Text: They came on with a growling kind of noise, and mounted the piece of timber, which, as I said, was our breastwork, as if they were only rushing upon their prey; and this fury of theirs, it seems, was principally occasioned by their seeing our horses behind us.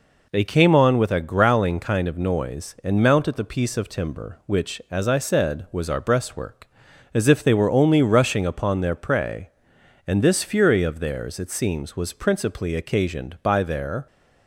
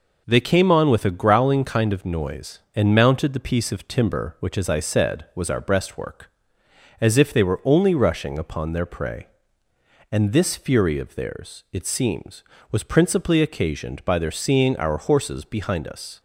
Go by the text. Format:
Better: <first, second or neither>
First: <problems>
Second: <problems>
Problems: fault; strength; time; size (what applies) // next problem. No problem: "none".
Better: second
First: stops before "seeing our horses behind us"; at 14.0 s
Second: none